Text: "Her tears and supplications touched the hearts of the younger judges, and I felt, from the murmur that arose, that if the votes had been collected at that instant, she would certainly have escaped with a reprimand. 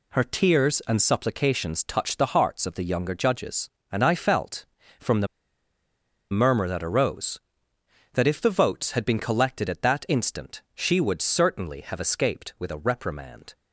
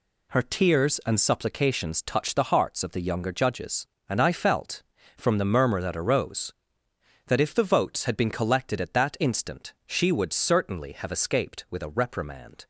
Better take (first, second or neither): second